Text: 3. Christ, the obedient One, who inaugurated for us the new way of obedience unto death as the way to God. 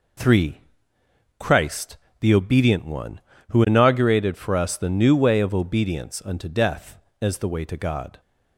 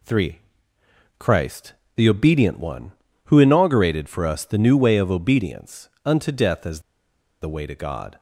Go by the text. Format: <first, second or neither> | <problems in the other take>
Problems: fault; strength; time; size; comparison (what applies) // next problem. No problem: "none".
first | pauses between "obedience" and "unto"; slight; at 5.8 s; 0.16 s long // pauses between "as" and "the"; noticeable; at 6.7 s; 0.62 s long